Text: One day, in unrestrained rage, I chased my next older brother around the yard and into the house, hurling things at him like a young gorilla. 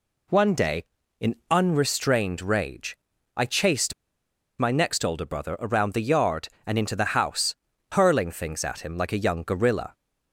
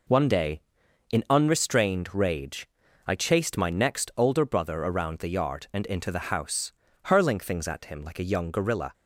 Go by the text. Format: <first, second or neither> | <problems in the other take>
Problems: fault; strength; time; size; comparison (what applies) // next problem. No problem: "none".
second | pauses between "chased" and "my"; noticeable; at 3.9 s; 0.65 s long